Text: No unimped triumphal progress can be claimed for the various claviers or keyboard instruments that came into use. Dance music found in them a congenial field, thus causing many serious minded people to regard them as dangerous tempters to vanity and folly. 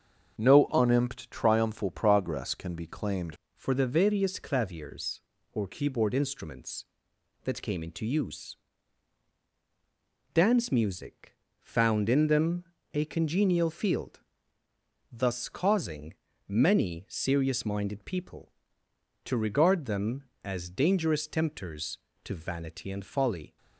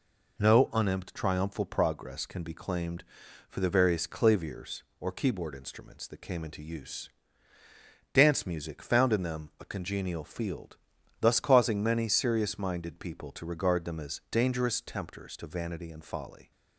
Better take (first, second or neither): second